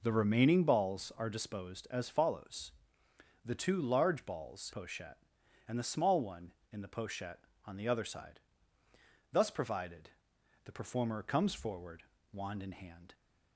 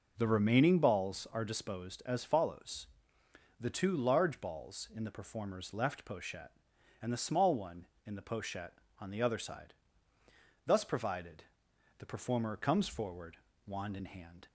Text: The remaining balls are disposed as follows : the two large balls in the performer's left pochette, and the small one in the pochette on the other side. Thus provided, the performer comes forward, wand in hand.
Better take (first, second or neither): second